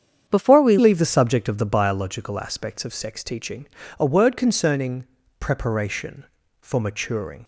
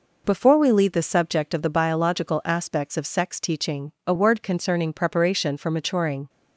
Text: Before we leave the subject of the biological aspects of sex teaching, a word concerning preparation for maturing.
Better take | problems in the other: second | starts louder than the rest; strong; until 1.2 s; 8 dB // changes voice at "leave"; from 0.7 s on; 6.7 s long // pauses between "concerning" and "preparation"; slight; at 5.0 s; 0.36 s long

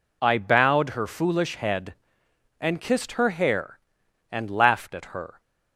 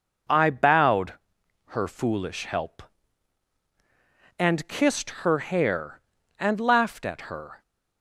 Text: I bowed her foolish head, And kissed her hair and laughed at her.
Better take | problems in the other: first | pauses between "bowed" and "her"; noticeable; at 1.1 s; 0.54 s long // says "help" for "head"; at 2.4 s

